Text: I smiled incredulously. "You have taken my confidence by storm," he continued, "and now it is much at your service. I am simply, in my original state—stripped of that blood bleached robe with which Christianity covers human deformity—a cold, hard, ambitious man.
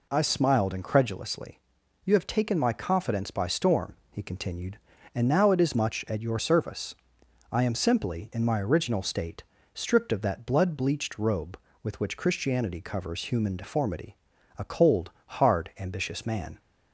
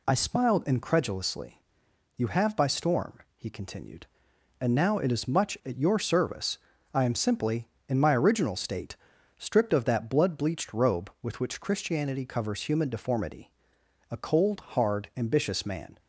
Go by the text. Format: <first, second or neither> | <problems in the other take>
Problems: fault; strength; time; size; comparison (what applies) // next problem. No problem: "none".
first | skips "taken my confidence"; at 2.5 s